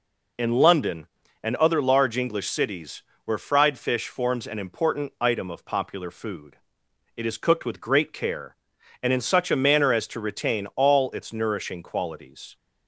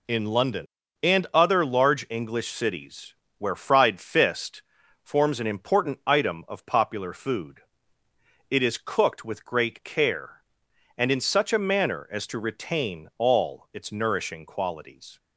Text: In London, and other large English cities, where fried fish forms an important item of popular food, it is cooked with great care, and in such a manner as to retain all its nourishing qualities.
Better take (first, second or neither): first